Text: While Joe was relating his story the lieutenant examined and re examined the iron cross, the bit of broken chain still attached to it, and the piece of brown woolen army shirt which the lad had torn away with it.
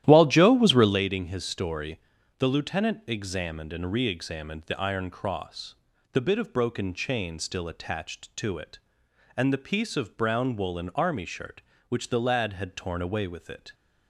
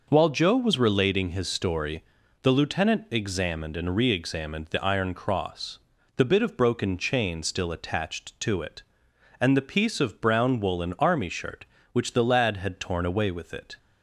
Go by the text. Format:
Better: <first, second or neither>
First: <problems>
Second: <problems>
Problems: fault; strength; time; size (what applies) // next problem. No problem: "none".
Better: second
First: starts louder than the rest; strong; until 1.0 s; 12.5 dB // pauses between "story" and "the"; at 1.9 s; 0.38 s long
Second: pauses between "story" and "the"; at 2.0 s; 0.38 s long